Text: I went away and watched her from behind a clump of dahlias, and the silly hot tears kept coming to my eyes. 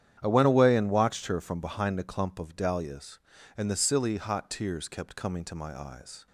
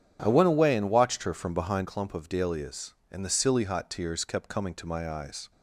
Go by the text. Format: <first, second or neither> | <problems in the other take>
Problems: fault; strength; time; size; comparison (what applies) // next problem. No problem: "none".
first | starts louder than the rest; strong; until 1.2 s; 9.5 dB; strong in the first // skips "a"; at 1.8 s